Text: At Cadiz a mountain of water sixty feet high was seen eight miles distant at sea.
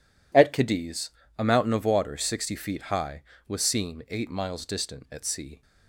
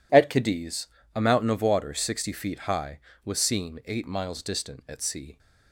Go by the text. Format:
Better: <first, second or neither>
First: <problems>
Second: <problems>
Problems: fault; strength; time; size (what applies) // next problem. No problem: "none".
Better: neither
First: pauses between "Cadiz" and "a"; slight; at 1.0 s; 0.28 s long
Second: pauses between "Cadiz" and "a"; slight; at 0.8 s; 0.28 s long